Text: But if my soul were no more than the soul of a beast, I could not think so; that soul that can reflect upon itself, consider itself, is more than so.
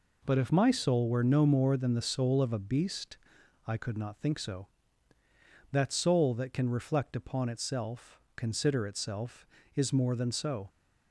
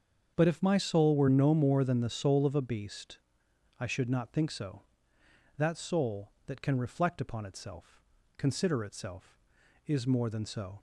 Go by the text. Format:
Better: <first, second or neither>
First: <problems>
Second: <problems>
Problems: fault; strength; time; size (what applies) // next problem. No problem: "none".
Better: first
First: none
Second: starts louder than the rest; strong; until 1.3 s; 7.5 dB // says "should" for "could"; at 3.8 s